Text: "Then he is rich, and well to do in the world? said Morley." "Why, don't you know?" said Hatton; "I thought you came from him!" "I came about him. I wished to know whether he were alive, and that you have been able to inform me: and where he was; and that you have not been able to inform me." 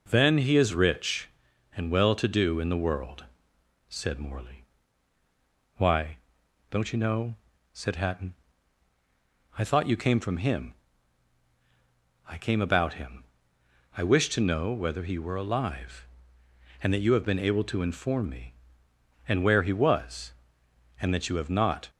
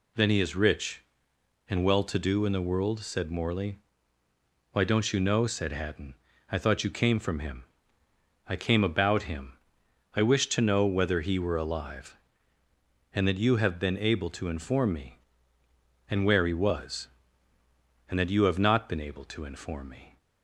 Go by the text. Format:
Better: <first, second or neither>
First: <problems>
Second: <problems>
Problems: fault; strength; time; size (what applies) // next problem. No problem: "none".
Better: second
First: stops before "been able to inform me"; at 21.8 s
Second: none